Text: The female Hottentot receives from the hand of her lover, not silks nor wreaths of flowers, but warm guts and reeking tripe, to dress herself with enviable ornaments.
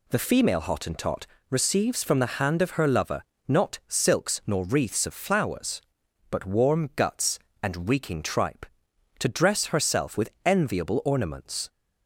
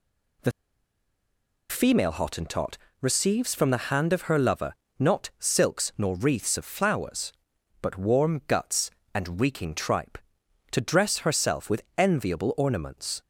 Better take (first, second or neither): first